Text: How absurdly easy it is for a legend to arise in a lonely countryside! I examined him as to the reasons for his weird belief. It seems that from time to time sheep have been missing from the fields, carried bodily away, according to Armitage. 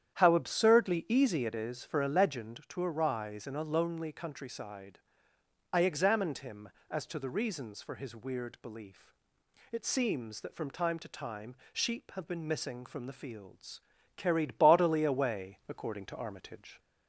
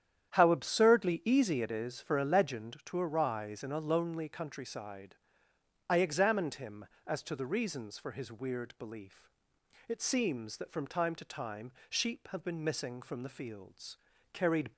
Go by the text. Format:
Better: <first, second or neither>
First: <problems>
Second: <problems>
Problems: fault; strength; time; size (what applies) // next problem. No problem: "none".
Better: first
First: starts louder than the rest; strong; until 1.1 s; 9.5 dB // pauses between "time" and "sheep"; slight; at 11.5 s; 0.18 s long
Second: starts louder than the rest; strong; until 1.3 s; 9.5 dB // pauses between "time" and "sheep"; slight; at 11.7 s; 0.18 s long // stops before "bodily away according to Armitage"; at 14.7 s